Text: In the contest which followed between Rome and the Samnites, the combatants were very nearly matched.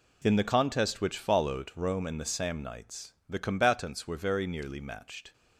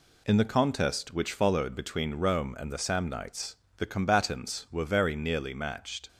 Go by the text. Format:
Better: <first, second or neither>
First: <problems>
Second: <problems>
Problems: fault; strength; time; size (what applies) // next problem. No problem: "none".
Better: second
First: skips "between"; at 1.7 s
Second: none